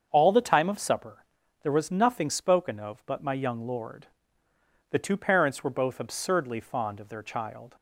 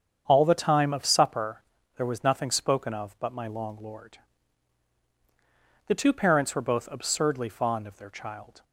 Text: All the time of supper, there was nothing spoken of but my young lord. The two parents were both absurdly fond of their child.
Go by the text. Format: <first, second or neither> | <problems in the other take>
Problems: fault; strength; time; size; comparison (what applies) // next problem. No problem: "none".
first | starts louder than the rest; strong; until 1.2 s; 7.5 dB; also in the first // says "long" for "young"; at 3.4 s